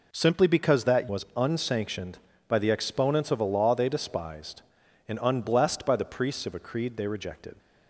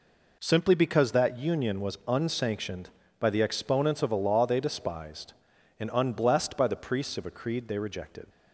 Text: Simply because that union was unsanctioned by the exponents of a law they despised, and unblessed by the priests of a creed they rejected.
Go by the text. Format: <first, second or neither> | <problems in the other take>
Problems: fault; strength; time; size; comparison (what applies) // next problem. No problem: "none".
second | skips "union"; at 1.0 s